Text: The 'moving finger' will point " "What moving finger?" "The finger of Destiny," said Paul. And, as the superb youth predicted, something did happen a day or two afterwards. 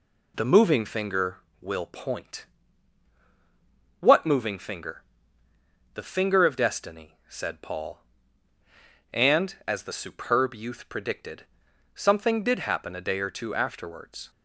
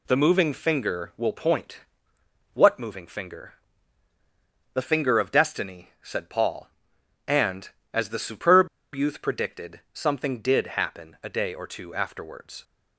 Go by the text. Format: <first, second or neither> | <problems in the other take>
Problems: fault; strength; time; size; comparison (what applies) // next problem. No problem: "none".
first | pauses between "superb" and "youth"; slight; at 8.6 s; 0.27 s long